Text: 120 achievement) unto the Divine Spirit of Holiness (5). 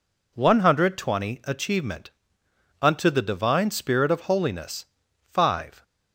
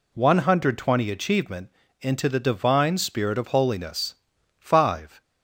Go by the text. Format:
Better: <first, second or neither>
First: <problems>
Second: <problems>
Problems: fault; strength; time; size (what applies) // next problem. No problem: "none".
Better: first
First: none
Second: says "into" for "unto"; at 1.9 s